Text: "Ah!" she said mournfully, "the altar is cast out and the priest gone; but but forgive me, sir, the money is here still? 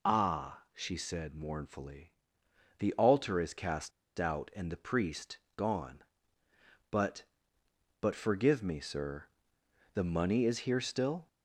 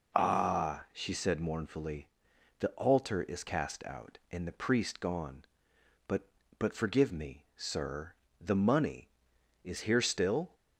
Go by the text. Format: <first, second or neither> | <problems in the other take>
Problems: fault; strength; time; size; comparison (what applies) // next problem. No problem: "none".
second | pauses between "cast" and "out"; slight; at 3.9 s; 0.28 s long // pauses between "priest" and "gone"; slight; at 5.3 s; 0.18 s long